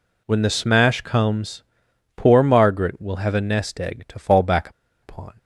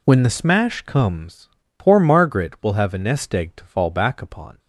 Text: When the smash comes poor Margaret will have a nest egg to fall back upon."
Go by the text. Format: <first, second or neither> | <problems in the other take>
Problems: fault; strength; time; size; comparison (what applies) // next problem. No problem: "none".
second | pauses between "comes" and "poor"; noticeable; at 1.6 s; 0.52 s long; slight in the second // pauses between "back" and "upon"; slight; at 4.6 s; 0.33 s long